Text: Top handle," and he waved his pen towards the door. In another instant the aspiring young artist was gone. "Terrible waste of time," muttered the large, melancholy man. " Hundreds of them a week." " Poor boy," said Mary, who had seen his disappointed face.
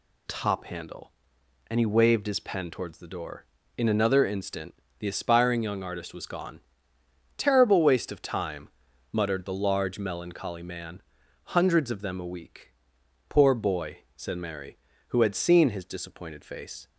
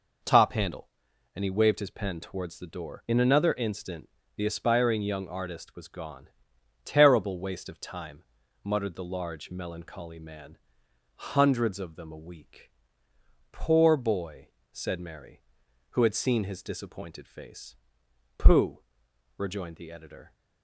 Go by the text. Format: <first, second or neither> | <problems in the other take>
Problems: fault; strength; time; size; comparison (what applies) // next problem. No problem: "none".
first | pauses between "instant" and "the"; slight; at 4.0 s; 0.28 s long; slight in the first // goes on to say "Pooh rejoined the editor"; strong; from 18.3 s on; 1.9 s long